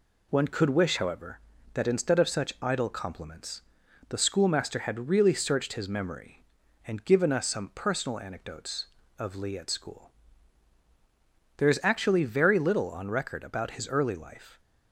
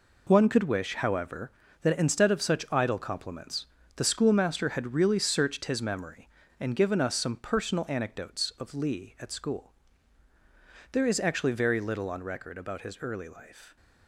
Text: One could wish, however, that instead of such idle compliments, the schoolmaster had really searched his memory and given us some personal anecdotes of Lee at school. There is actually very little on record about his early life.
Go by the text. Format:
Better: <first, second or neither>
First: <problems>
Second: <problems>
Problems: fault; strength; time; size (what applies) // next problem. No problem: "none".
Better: first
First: none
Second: gets quieter; strong; throughout; 9.5 dB